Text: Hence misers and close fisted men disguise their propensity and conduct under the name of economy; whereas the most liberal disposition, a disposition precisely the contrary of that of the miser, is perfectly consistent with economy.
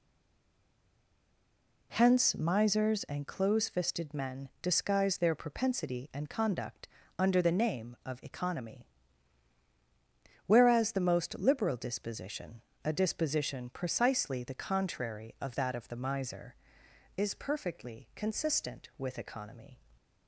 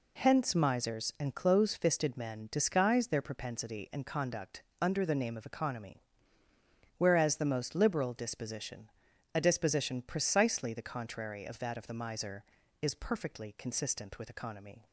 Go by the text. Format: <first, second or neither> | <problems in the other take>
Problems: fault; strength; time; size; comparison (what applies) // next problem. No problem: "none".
second | stays silent before the first word; noticeable; until 1.9 s; 1.9 s long // pauses between "conduct" and "under"; slight; at 6.8 s; 0.32 s long; slight in the second